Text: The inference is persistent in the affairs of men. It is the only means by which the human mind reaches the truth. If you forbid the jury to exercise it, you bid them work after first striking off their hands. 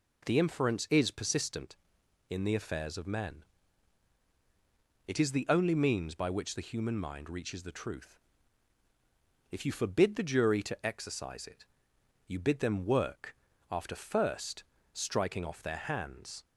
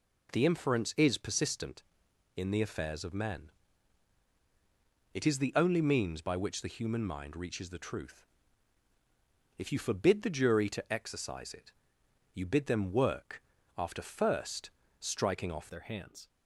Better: first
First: pauses between "work" and "after"; slight; at 13.3 s; 0.34 s long // pauses between "first" and "striking"; slight; at 14.6 s; 0.30 s long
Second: pauses between "work" and "after"; slight; at 13.4 s; 0.34 s long // pauses between "first" and "striking"; slight; at 14.7 s; 0.30 s long // changes voice at "their"; from 15.6 s on; 0.6 s long

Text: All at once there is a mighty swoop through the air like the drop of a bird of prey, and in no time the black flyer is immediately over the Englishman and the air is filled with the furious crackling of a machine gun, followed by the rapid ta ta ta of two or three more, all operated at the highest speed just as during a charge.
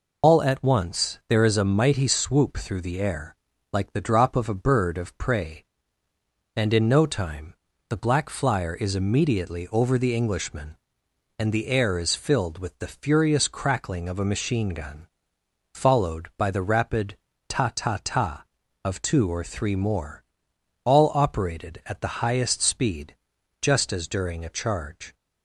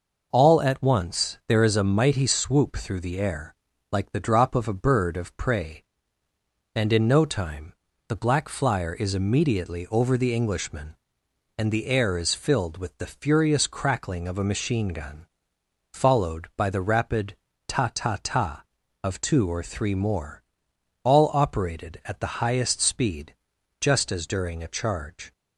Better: second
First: loses the start of "All"; at 0.2 s; 115 ms // pauses between "air" and "like"; at 3.3 s; 0.38 s long // pauses between "time" and "the"; slight; at 7.5 s; 0.34 s long // pauses between "rapid" and "ta"; slight; at 17.1 s; 0.32 s long // pauses between "speed" and "just"; noticeable; at 23.1 s; 0.46 s long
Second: pauses between "air" and "like"; at 3.5 s; 0.38 s long // pauses between "time" and "the"; slight; at 7.7 s; 0.34 s long // pauses between "rapid" and "ta"; slight; at 17.3 s; 0.32 s long // pauses between "speed" and "just"; noticeable; at 23.3 s; 0.46 s long

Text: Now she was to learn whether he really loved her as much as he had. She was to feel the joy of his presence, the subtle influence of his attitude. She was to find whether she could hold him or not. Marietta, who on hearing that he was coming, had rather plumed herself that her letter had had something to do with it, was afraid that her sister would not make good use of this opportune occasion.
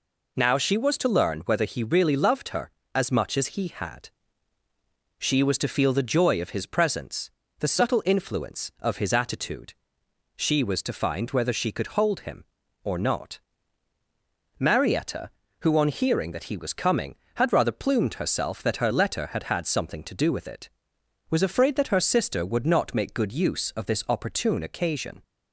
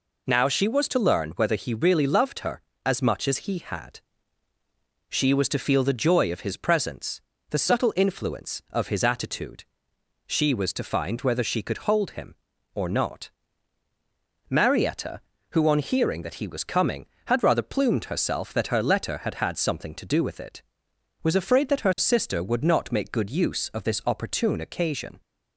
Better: neither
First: none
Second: none

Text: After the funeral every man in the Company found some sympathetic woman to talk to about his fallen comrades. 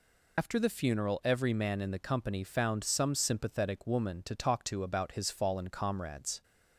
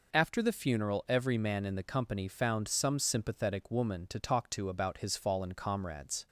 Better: second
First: loses the start of "After"; at 0.3 s; 80 ms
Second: none

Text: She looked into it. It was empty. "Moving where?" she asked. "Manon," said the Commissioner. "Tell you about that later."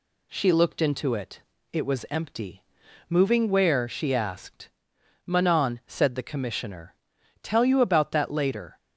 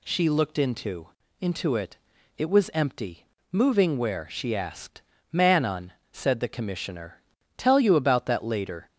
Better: first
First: none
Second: says "into" twice; at 1.4 s

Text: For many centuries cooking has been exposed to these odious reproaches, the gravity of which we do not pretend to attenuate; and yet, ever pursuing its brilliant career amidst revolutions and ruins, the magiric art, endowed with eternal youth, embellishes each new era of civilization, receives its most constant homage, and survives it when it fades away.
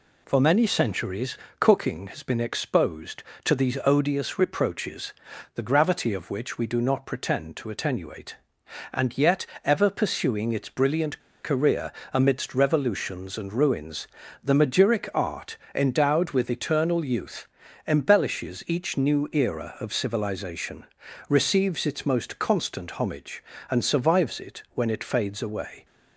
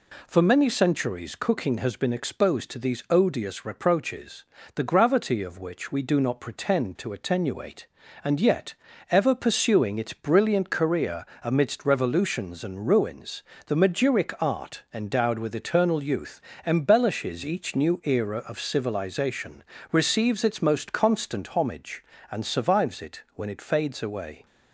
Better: second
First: pauses between "centuries" and "cooking"; slight; at 1.3 s; 0.22 s long // pauses between "brilliant" and "career"; slight; at 11.1 s; 0.24 s long // pauses between "career" and "amidst"; slight; at 11.9 s; 0.22 s long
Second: pauses between "career" and "amidst"; slight; at 11.2 s; 0.18 s long

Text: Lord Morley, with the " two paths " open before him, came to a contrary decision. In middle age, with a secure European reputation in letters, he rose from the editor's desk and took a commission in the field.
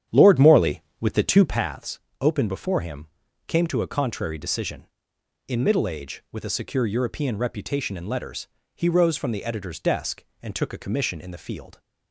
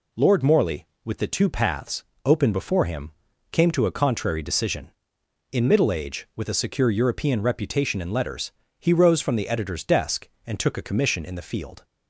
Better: second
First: starts louder than the rest; strong; until 1.6 s; 9.5 dB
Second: none

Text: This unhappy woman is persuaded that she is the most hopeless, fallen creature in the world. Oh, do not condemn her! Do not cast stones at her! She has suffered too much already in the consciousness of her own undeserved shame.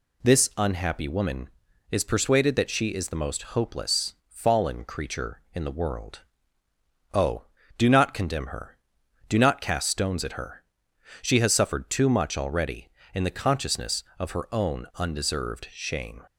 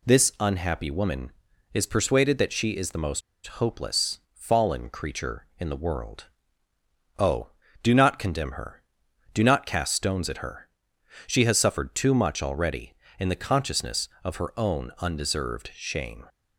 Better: first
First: none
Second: pauses between "most" and "hopeless"; slight; at 3.2 s; 0.25 s long

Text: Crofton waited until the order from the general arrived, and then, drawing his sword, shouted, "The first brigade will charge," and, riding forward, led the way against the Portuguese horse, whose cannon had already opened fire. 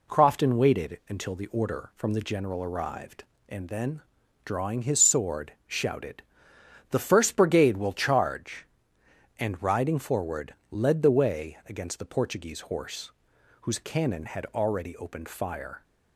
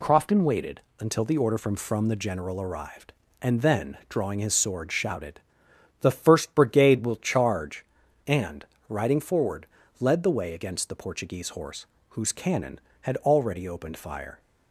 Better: first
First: none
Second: pauses between "waited" and "until"; slight; at 0.7 s; 0.18 s long // says "from" twice; at 1.7 s

